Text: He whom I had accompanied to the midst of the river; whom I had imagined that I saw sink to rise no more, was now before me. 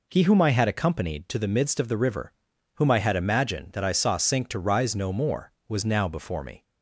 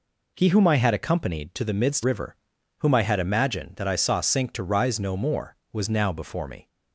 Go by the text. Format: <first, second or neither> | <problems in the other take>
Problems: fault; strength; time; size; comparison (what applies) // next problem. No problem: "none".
first | skips "of the"; at 2.0 s